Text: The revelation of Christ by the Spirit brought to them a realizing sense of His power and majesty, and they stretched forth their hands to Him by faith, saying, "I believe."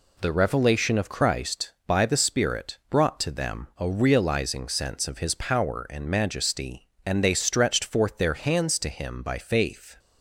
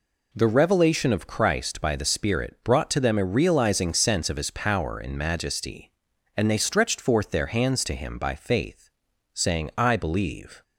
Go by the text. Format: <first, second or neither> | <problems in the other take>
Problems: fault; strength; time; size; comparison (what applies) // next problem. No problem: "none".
second | stops before "saying I believe"; at 9.9 s